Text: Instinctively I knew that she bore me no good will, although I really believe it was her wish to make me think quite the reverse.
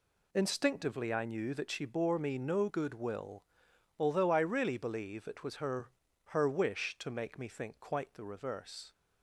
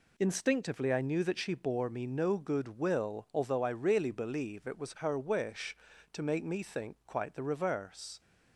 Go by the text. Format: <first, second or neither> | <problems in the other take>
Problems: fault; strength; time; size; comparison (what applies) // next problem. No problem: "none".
second | says "her" twice; at 6.3 s